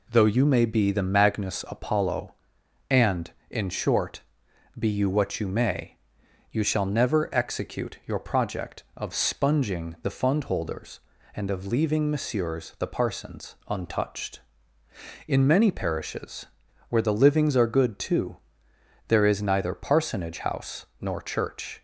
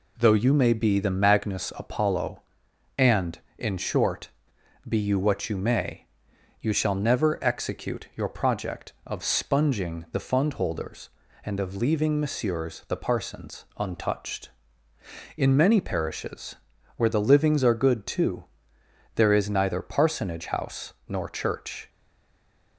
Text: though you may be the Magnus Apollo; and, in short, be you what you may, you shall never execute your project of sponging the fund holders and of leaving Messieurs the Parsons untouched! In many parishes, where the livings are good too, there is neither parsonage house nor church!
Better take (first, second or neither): first